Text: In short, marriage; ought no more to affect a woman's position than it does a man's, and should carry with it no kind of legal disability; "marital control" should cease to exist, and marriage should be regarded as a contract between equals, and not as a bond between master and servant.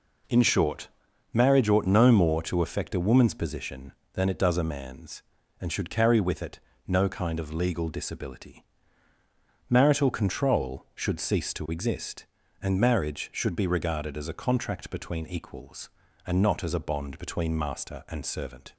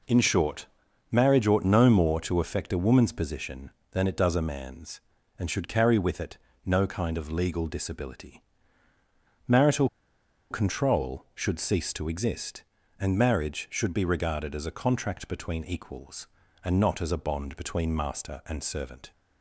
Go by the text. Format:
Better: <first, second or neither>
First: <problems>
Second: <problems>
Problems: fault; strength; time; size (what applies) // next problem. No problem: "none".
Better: first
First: pauses between "it" and "no"; slight; at 6.5 s; 0.28 s long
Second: pauses between "it" and "no"; slight; at 6.3 s; 0.28 s long // pauses between "marital" and "control"; noticeable; at 9.8 s; 0.63 s long